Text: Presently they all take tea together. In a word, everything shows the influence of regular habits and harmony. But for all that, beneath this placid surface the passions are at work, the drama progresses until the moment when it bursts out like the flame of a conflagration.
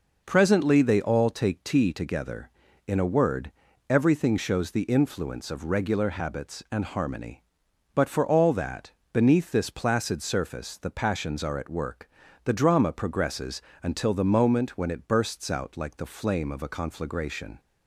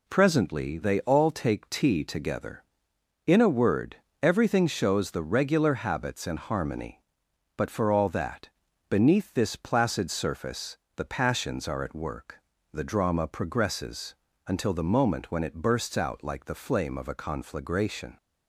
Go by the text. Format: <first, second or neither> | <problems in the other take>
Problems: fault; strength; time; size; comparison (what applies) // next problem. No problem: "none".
first | skips "influence of"; at 5.2 s // pauses between "surface" and "the"; slight; at 10.7 s; 0.20 s long // pauses between "progresses" and "until"; slight; at 14.1 s; 0.32 s long; slight in the first